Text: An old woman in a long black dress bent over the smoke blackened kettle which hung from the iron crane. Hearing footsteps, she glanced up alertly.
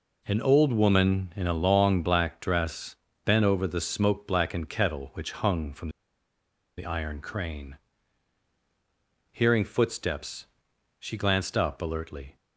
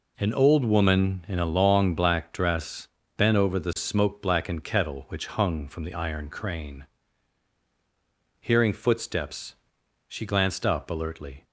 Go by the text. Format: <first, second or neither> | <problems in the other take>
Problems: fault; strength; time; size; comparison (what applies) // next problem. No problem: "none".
second | pauses between "dress" and "bent"; slight; at 2.9 s; 0.30 s long; slight in the second // pauses between "from" and "the"; noticeable; at 5.8 s; 0.88 s long